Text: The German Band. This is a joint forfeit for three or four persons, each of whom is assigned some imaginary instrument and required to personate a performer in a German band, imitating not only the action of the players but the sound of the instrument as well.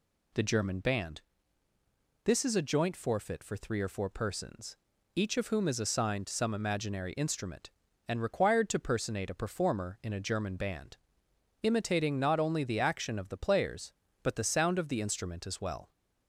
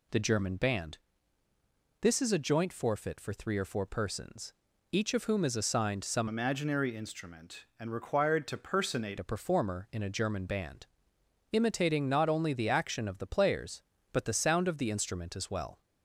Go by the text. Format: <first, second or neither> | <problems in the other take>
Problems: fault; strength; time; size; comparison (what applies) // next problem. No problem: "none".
first | changes voice from "imaginary" to "personate"; from 6.2 to 9.1 s; 2.9 s long